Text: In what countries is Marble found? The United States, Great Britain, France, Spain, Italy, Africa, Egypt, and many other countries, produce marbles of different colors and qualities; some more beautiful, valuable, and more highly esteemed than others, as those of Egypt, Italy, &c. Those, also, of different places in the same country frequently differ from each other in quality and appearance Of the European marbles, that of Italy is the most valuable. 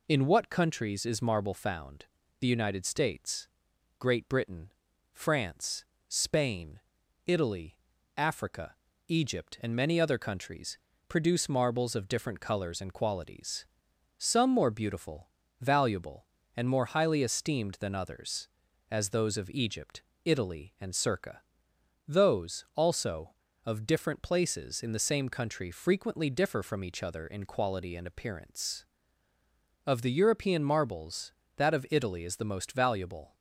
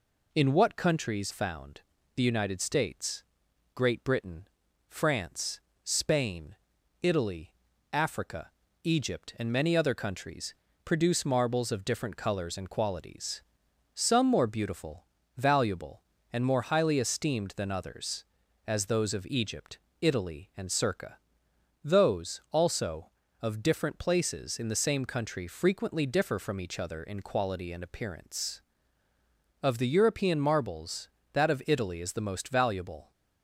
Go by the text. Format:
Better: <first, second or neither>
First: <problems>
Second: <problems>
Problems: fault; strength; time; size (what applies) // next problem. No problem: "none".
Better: first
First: none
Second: skips "is Marble"; at 1.3 s